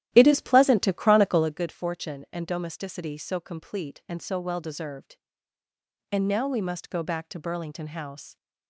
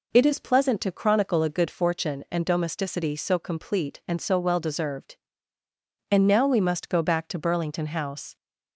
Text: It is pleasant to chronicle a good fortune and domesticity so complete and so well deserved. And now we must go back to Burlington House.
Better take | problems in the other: second | starts louder than the rest; strong; until 1.5 s; 12.5 dB

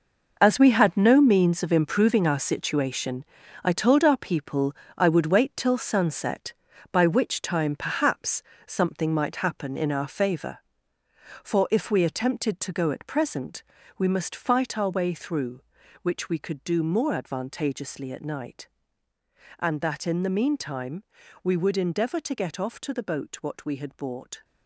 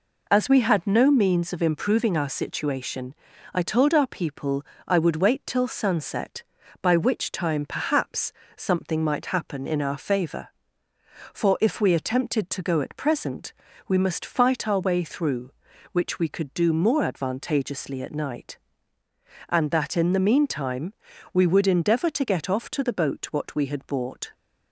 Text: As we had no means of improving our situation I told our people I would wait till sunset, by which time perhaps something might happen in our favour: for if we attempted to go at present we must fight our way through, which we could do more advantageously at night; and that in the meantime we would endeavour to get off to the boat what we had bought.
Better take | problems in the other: second | gets quieter; strong; throughout; 11 dB // pauses between "situation" and "I"; at 3.2 s; 0.40 s long; also in the second // pauses between "people" and "I"; slight; at 4.7 s; 0.22 s long; slight in the second // pauses between "perhaps" and "something"; slight; at 8.4 s; 0.20 s long; slight in the second // pauses between "present" and "we"; slight; at 13.6 s; 0.34 s long; slight in the second // pauses between "meantime" and "we"; at 21.0 s; 0.40 s long; also in the second

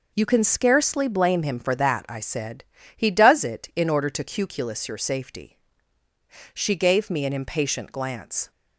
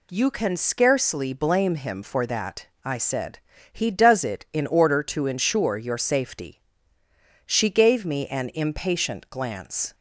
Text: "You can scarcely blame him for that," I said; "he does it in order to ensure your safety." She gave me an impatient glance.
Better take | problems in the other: second | says "cuculus" for "ensure"; at 4.2 s

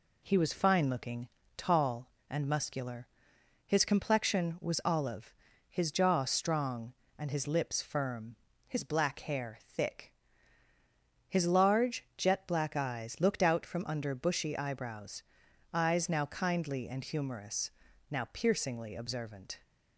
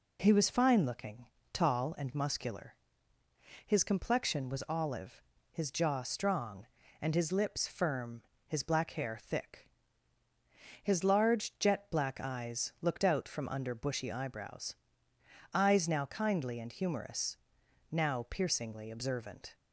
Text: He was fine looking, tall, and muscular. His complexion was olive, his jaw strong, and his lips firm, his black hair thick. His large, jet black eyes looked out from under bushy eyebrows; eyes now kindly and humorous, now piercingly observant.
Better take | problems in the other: neither | none

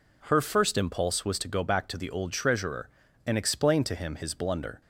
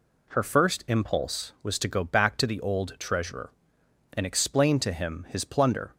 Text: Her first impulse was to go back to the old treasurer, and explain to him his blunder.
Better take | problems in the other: first | says "plunder" for "blunder"; at 5.4 s

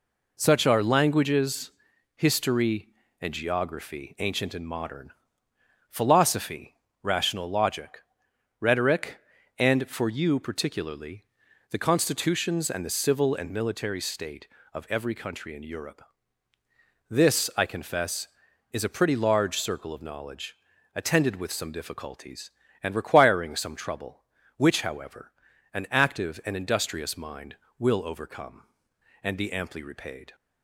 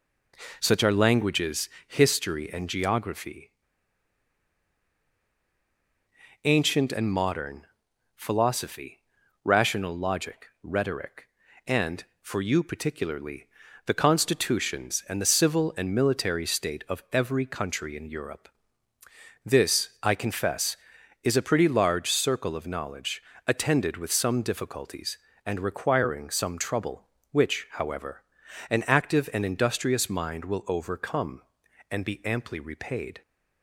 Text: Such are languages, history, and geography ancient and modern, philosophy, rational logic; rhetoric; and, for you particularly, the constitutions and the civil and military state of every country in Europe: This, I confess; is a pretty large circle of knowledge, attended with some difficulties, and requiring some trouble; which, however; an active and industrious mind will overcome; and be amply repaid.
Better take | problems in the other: first | pauses between "geography" and "ancient"; strong; at 3.5 s; 2.9 s long

